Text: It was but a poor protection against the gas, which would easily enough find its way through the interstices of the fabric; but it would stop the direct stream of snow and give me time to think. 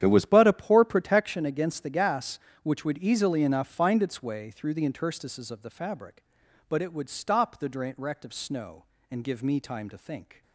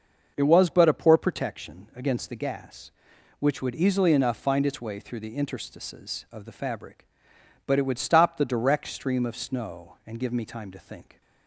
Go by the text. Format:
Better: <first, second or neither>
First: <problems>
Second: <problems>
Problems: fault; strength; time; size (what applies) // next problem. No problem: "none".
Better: second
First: starts louder than the rest; strong; until 1.0 s; 10 dB // skips "stream"; at 8.2 s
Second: starts louder than the rest; noticeable; until 1.3 s; 6 dB